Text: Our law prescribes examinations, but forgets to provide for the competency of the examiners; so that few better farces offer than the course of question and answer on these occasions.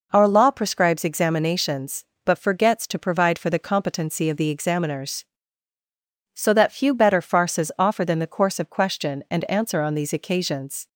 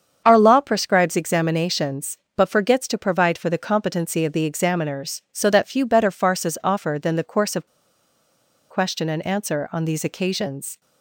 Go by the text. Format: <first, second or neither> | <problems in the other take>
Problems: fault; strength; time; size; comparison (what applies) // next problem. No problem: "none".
first | starts louder than the rest; strong; until 1.2 s; 7.5 dB // pauses between "of" and "question"; at 7.6 s; 1.0 s long